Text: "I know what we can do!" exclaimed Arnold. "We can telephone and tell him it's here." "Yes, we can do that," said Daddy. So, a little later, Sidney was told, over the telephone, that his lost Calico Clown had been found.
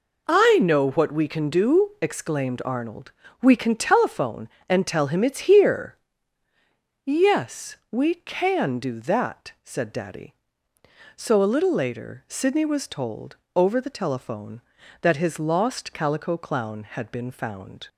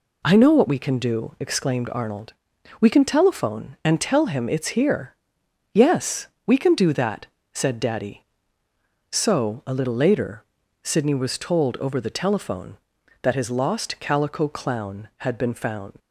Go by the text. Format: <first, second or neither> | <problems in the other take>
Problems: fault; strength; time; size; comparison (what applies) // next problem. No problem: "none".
first | leaves "found" unfinished; at 16.0 s; 55 ms